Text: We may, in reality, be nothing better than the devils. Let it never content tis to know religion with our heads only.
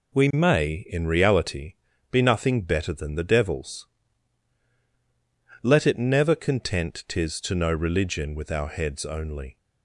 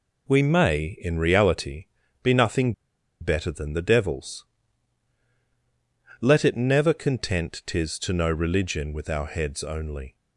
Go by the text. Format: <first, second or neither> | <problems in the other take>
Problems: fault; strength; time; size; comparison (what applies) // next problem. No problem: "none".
first | pauses between "nothing" and "better"; noticeable; at 2.7 s; 0.48 s long